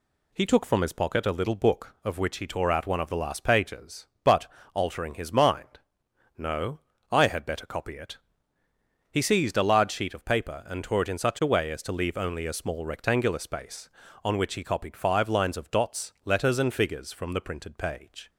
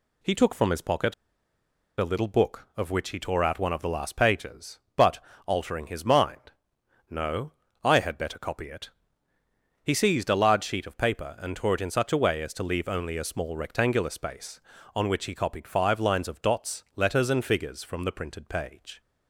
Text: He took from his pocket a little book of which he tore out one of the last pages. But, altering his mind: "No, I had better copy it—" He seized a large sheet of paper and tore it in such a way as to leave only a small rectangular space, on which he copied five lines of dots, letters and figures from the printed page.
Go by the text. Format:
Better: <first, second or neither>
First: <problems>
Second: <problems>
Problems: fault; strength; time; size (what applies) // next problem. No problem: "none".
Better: first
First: none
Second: pauses between "pocket" and "a"; noticeable; at 1.1 s; 0.85 s long